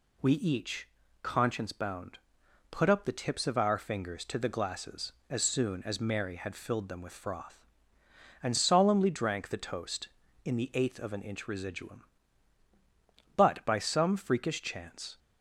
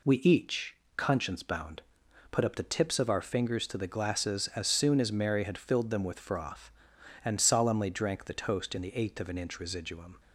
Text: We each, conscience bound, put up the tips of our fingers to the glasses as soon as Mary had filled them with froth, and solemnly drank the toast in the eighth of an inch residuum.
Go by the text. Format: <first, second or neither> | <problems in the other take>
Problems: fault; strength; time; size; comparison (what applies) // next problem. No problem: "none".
second | goes on to say "But by some freakish chance"; strong; from 13.3 s on; 1.8 s long